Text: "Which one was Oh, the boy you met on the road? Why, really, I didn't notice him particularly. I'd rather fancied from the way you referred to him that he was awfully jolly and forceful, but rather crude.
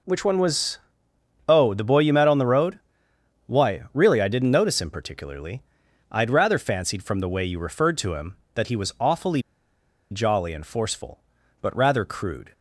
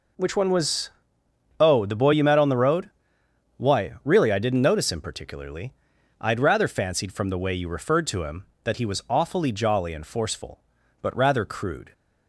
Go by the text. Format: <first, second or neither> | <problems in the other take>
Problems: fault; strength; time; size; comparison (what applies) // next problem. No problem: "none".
second | pauses between "was" and "Oh"; noticeable; at 0.7 s; 0.68 s long; noticeable in the second // pauses between "awfully" and "jolly"; noticeable; at 9.4 s; 0.70 s long